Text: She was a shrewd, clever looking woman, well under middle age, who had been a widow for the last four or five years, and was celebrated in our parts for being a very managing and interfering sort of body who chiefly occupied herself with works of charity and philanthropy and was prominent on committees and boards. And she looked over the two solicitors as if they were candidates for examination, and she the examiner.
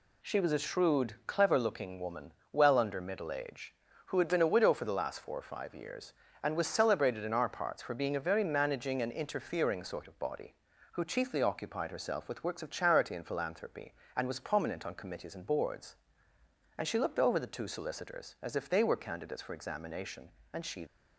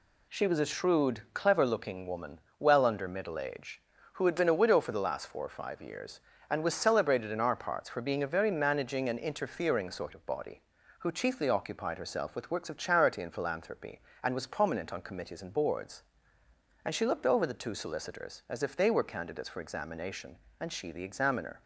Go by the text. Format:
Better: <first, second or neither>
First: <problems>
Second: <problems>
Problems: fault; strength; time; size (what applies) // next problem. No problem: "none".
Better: second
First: stops before "the examiner"; at 20.8 s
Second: none